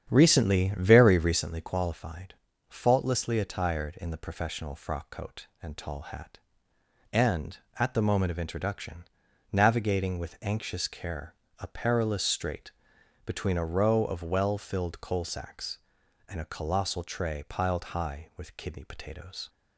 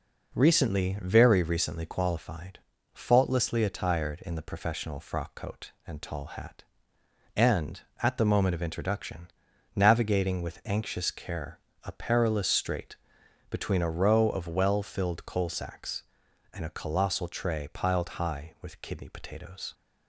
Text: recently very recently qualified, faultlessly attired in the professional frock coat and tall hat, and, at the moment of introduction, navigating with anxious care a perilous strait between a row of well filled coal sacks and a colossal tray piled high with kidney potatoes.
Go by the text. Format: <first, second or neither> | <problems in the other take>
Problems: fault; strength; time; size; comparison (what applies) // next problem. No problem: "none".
second | starts louder than the rest; strong; until 1.5 s; 8.5 dB // pauses between "care" and "a"; slight; at 11.3 s; 0.26 s long; slight in the second // pauses between "strait" and "between"; noticeable; at 12.7 s; 0.54 s long; noticeable in the second